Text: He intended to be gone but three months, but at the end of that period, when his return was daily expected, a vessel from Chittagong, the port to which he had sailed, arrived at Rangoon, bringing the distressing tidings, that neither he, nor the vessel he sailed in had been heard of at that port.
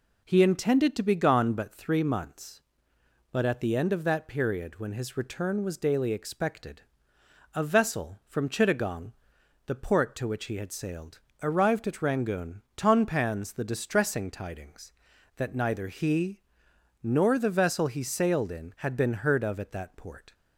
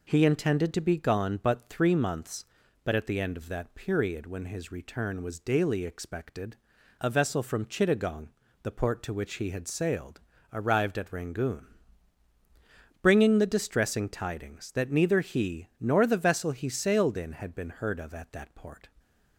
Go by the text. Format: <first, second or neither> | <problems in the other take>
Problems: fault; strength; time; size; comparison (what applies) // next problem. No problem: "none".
second | says "tonpans" for "bringing"; at 12.7 s